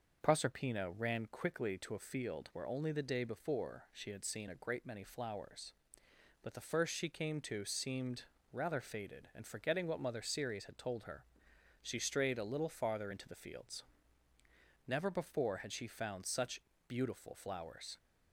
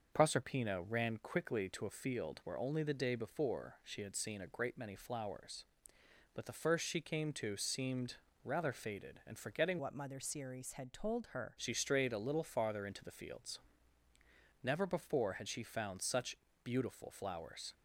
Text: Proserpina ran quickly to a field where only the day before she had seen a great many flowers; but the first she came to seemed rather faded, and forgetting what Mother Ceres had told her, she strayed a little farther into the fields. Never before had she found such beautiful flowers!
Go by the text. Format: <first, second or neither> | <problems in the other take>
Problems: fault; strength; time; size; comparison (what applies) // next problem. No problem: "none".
first | starts louder than the rest; until 1.1 s; 6 dB; also in the first // pauses between "seemed" and "rather"; slight; at 8.1 s; 0.28 s long; slight in the first // changes voice from "what" to "her"; from 9.7 to 11.5 s; 1.8 s long // pauses between "such" and "beautiful"; slight; at 16.3 s; 0.30 s long; slight in the first